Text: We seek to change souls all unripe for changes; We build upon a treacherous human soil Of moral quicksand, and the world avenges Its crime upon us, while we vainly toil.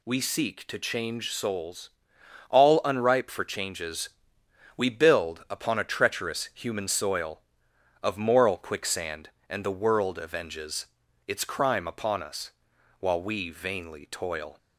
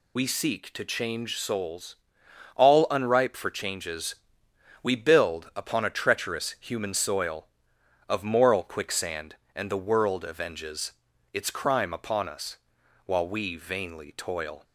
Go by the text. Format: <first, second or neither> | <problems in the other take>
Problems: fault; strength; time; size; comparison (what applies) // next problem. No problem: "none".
first | loses the start of "We"; at 0.1 s; 60 ms // pauses between "souls" and "all"; noticeable; at 1.9 s; 0.60 s long; noticeable in the first // pauses between "avenges" and "Its"; at 10.9 s; 0.40 s long; also in the first